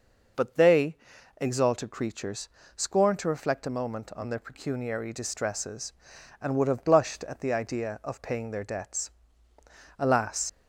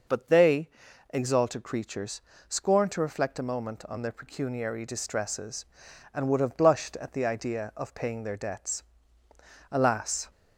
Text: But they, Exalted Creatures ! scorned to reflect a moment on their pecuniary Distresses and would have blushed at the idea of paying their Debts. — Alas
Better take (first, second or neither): second